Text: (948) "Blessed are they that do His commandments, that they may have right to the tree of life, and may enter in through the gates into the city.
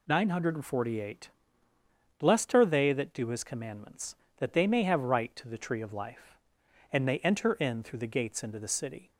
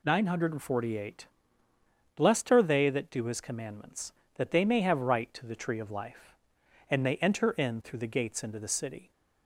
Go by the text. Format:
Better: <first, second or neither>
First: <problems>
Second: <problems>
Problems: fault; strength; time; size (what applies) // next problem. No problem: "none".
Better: neither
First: none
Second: none